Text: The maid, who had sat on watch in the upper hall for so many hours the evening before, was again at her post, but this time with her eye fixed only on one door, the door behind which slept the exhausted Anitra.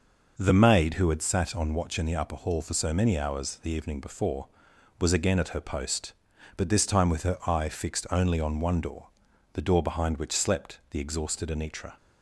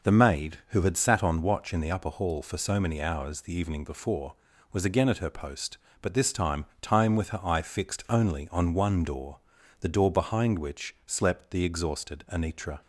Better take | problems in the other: first | says "time" twice; at 6.8 s

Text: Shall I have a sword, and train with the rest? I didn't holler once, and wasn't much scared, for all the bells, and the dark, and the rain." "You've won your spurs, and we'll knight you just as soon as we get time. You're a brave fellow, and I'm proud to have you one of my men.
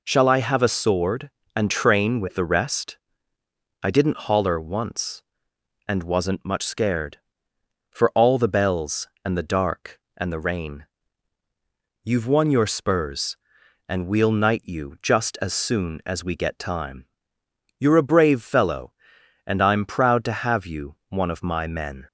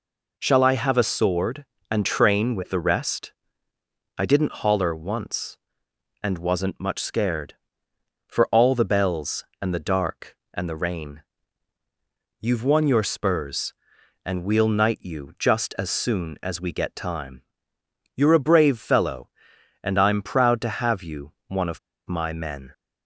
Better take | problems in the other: first | pauses between "you" and "one"; slight; at 21.3 s; 0.16 s long // pauses between "of" and "my"; slight; at 21.7 s; 0.29 s long

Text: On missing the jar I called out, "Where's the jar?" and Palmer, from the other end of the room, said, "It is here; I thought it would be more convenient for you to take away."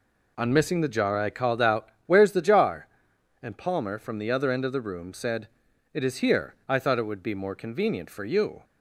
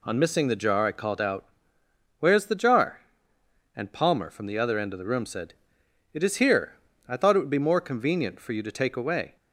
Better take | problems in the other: second | stops before "to take away"; at 8.6 s

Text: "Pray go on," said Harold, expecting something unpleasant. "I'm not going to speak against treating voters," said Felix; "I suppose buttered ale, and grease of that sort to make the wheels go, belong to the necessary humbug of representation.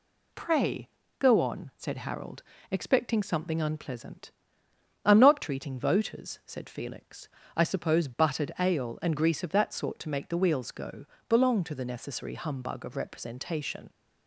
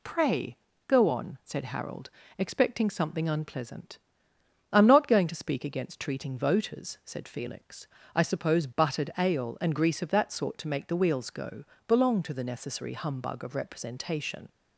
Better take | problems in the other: second | pauses between "Pray" and "go"; slight; at 0.8 s; 0.30 s long; slight in the second // skips "going to speak against"; at 5.4 s

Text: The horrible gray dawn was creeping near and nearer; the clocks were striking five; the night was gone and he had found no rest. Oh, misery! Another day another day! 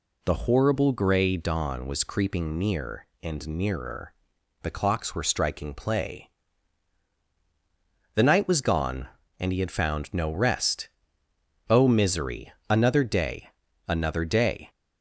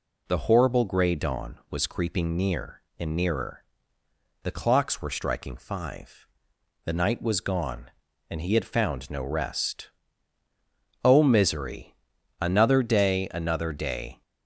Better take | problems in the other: second | says "play" for "five"; at 5.7 s // pauses between "day" and "another"; at 13.4 s; 0.38 s long

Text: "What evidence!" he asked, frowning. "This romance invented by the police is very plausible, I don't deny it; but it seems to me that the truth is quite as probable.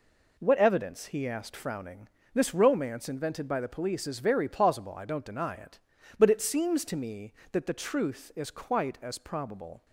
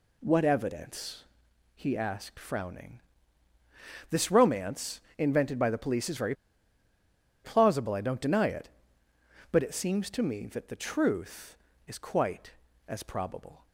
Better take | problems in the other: first | pauses between "romance" and "invented"; slight; at 4.9 s; 0.20 s long // pauses between "very" and "plausible"; at 6.3 s; 1.1 s long

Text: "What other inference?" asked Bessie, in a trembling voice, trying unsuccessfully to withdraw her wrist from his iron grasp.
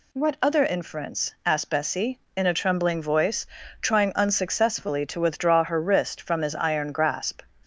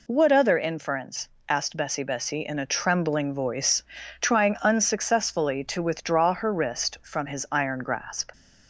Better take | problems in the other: first | says "Bessie" twice; at 2.0 s

